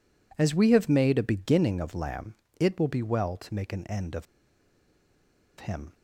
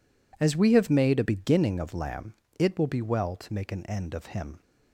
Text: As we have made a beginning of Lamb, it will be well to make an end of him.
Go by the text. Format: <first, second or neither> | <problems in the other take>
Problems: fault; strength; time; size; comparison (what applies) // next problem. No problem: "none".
second | pauses between "of" and "him"; strong; at 4.2 s; 1.3 s long